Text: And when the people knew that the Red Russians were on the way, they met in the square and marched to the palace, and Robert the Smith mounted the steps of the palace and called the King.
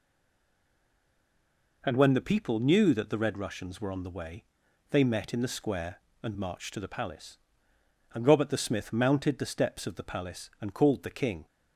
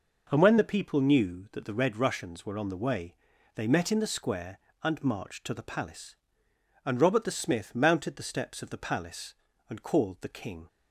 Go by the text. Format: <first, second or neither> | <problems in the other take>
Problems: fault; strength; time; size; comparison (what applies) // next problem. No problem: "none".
second | stays silent before the first word; noticeable; until 1.8 s; 1.8 s long